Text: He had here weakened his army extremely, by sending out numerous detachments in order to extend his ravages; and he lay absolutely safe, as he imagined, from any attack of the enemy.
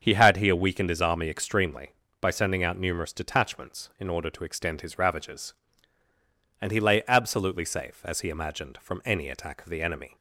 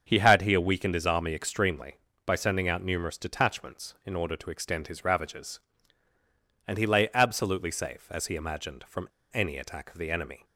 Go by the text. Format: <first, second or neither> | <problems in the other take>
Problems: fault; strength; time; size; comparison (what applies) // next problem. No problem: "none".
first | starts louder than the rest; until 1.0 s; 7 dB; also in the first // pauses between "from" and "any"; slight; at 9.0 s; 0.22 s long